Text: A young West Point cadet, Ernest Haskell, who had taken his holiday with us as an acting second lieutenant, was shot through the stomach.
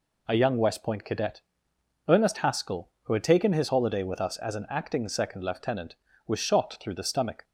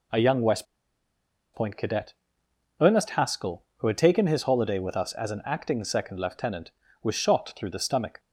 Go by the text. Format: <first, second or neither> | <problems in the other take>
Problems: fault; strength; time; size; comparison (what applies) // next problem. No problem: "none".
first | pauses between "West" and "Point"; noticeable; at 0.6 s; 0.88 s long